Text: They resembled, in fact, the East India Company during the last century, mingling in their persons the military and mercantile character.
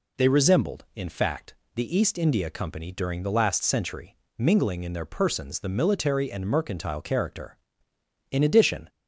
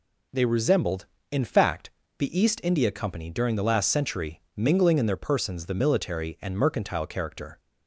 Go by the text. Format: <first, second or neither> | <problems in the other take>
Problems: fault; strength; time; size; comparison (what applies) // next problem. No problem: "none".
second | goes on to say "In addition"; from 8.3 s on; 0.58 s long